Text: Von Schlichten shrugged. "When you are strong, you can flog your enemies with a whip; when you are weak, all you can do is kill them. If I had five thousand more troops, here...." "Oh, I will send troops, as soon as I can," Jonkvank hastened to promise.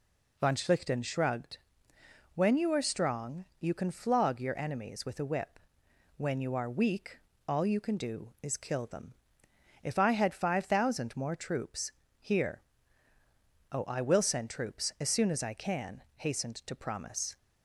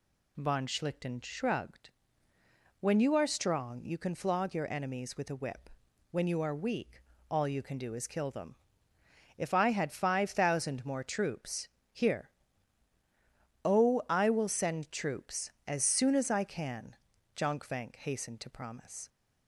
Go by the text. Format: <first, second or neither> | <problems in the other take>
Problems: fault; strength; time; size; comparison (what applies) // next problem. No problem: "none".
second | skips "Jonkvank"; at 16.0 s